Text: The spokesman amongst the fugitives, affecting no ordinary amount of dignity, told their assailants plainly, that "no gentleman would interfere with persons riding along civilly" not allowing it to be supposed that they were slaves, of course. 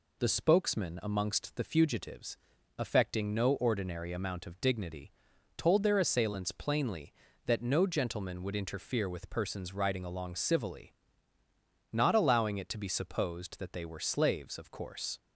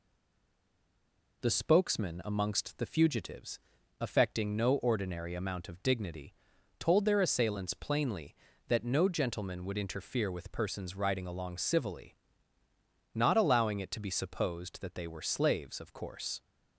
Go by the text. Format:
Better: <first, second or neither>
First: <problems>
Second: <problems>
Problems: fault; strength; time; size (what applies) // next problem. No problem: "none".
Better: first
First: pauses between "civilly" and "not"; noticeable; at 10.9 s; 0.98 s long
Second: stays silent before the first word; noticeable; until 1.4 s; 1.4 s long // pauses between "civilly" and "not"; noticeable; at 12.1 s; 0.98 s long